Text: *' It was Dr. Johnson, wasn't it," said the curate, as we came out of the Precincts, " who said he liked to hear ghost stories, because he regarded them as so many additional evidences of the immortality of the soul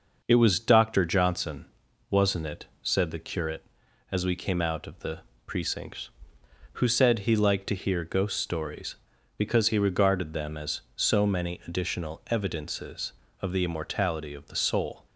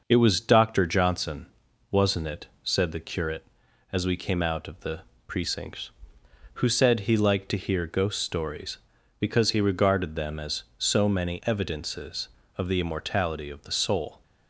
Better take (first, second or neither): first